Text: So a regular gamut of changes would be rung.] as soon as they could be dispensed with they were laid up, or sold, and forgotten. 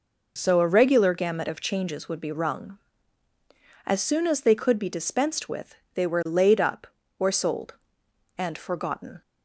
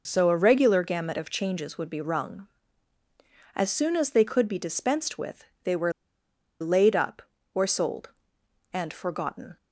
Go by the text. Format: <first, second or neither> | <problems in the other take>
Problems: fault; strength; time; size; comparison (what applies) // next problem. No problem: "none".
first | pauses between "with" and "they"; slight; at 5.4 s; 0.18 s long; slight in the first // pauses between "were" and "laid"; noticeable; at 5.9 s; 0.68 s long